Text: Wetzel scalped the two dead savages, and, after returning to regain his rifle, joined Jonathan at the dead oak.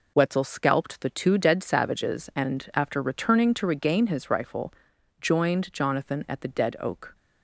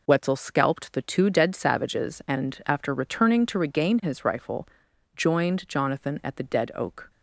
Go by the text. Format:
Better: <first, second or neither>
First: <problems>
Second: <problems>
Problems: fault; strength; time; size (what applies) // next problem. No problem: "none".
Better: neither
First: none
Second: none